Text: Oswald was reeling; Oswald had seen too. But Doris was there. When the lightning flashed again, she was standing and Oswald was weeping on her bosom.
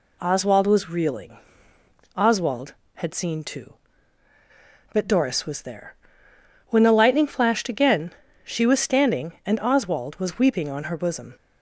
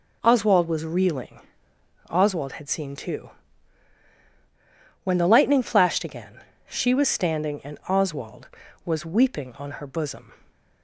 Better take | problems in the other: first | skips "But Doris was there"; at 4.1 s

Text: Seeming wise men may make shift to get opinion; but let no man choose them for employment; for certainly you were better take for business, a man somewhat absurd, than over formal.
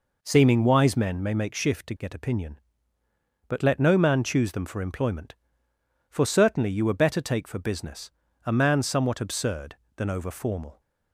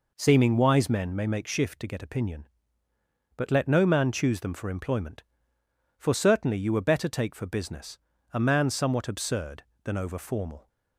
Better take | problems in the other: neither | none

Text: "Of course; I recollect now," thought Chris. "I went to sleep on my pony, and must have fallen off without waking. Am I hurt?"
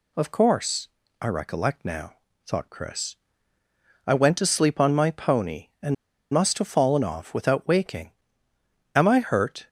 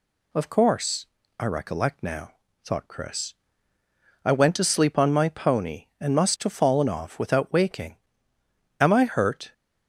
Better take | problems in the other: second | pauses between "and" and "must"; at 5.9 s; 0.36 s long

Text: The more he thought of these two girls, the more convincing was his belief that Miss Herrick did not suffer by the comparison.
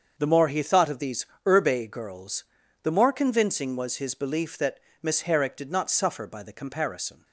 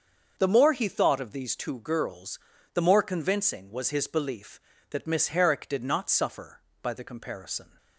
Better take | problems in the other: second | starts louder than the rest; until 1.1 s; 6.5 dB; also in the second // says "urbe" for "two"; at 1.4 s // pauses between "that" and "Miss"; slight; at 4.7 s; 0.22 s long

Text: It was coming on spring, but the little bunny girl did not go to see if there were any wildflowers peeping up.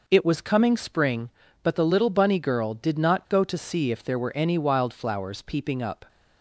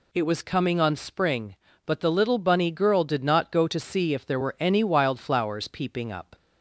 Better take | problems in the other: second | skips "on"; at 0.7 s

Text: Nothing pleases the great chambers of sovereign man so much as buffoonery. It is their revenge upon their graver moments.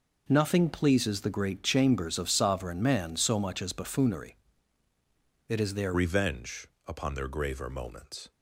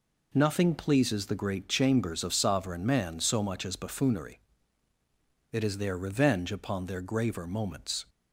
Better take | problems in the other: second | changes voice at "revenge"; from 5.9 s on; 2.4 s long // pauses between "revenge" and "upon"; slight; at 6.6 s; 0.20 s long

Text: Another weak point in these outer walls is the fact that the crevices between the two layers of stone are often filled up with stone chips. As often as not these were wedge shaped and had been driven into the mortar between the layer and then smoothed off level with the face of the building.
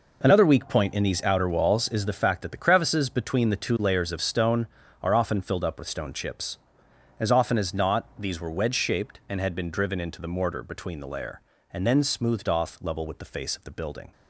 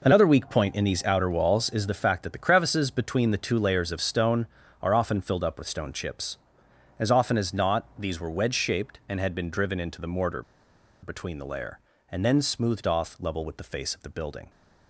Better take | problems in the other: first | pauses between "mortar" and "between"; noticeable; at 10.4 s; 0.59 s long

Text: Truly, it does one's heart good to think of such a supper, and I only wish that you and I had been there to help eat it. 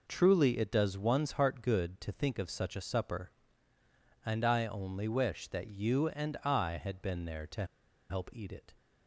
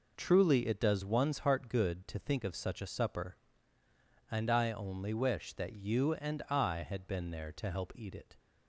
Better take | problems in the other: second | pauses between "to" and "help"; at 7.6 s; 0.45 s long

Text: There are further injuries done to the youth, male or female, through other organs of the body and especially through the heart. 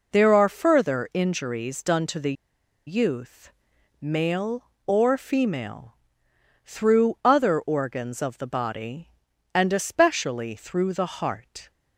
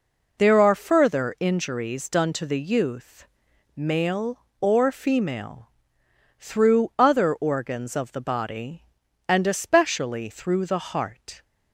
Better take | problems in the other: second | pauses between "the" and "youth"; noticeable; at 2.3 s; 0.53 s long

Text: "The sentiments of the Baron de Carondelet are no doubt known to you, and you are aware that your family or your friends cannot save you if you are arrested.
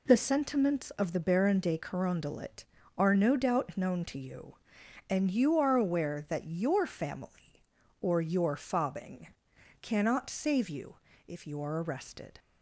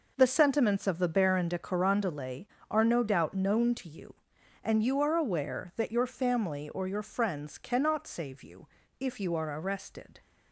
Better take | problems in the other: second | says "fobbing" for "friends"; at 8.5 s // pauses between "you" and "if"; slight; at 10.9 s; 0.32 s long; slight in the second

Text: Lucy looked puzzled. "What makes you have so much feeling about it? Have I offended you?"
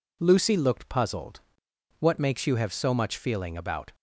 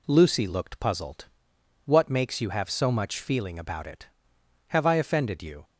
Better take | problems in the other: second | stops before "it Have I offended you"; at 3.9 s

